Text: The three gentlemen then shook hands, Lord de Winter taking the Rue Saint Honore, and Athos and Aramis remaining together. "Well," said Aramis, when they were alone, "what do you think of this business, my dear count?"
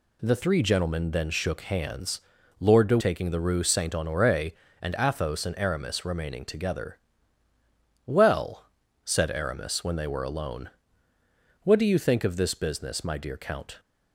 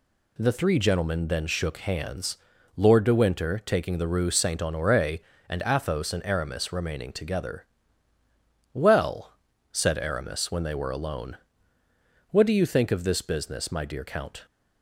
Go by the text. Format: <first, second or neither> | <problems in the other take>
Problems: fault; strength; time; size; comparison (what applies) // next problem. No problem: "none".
second | skips "Winter"; at 2.9 s